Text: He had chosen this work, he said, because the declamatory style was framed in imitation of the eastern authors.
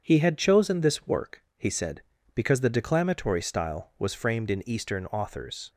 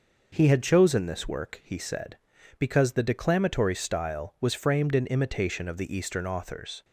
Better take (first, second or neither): second